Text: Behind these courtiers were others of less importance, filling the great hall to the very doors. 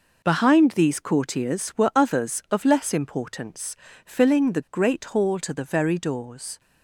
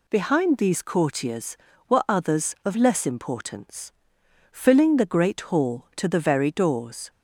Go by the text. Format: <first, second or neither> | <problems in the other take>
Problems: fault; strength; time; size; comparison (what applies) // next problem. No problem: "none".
second | gets quieter; strong; throughout; 10 dB